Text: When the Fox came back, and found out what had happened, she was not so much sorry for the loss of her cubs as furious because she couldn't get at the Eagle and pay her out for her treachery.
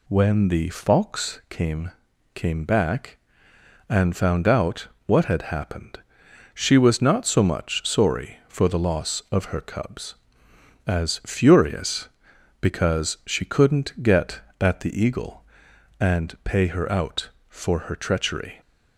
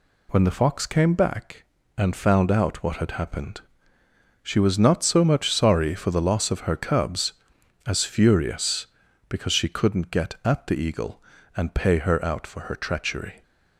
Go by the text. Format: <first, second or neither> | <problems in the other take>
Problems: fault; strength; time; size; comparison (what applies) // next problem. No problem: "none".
second | says "came" twice; at 2.3 s // pauses between "out" and "what"; slight; at 4.8 s; 0.20 s long